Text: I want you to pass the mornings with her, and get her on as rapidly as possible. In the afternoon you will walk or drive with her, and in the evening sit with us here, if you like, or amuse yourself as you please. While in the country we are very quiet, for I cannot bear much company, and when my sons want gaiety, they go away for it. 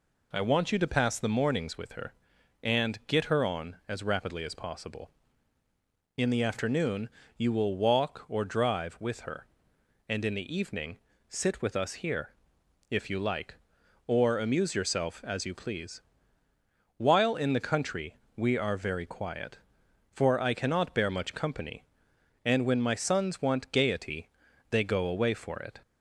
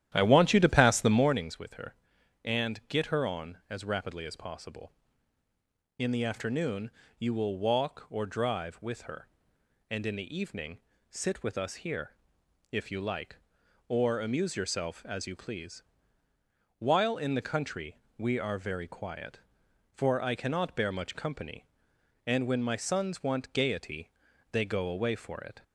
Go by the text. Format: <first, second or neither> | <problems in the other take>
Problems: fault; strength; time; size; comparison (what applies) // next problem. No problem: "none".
first | starts louder than the rest; strong; until 1.5 s; 11.5 dB // pauses between "afternoon" and "you"; slight; at 6.8 s; 0.28 s long; slight in the first // pauses between "evening" and "sit"; slight; at 10.7 s; 0.30 s long; slight in the first // pauses between "country" and "we"; slight; at 17.9 s; 0.22 s long; slight in the first